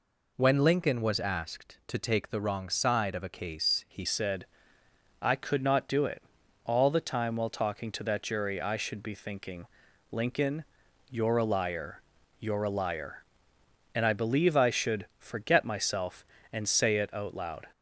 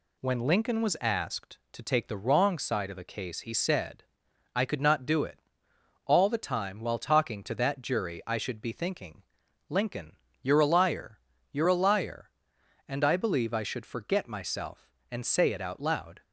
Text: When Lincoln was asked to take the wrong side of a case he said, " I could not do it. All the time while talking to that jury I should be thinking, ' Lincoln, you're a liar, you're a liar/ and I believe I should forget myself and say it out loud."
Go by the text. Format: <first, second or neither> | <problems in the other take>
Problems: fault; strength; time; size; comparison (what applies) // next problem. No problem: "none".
second | changes voice at "said"; from 4.0 s on; 13.6 s long